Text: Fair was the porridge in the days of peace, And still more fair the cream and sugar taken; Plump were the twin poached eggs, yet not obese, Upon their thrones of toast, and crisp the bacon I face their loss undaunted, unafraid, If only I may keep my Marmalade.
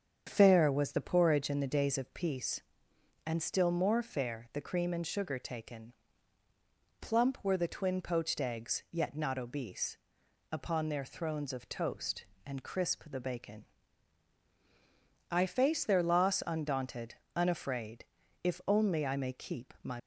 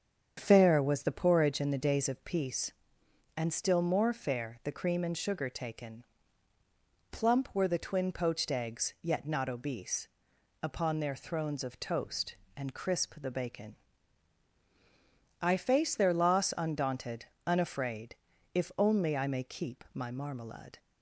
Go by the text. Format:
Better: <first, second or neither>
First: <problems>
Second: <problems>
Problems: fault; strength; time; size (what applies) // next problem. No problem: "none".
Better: second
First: starts louder than the rest; strong; until 1.2 s; 7.5 dB // pauses between "bacon" and "I"; strong; at 13.6 s; 1.6 s long // stops before "Marmalade"; at 19.9 s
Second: starts louder than the rest; strong; until 1.3 s; 7.5 dB // pauses between "bacon" and "I"; strong; at 13.7 s; 1.6 s long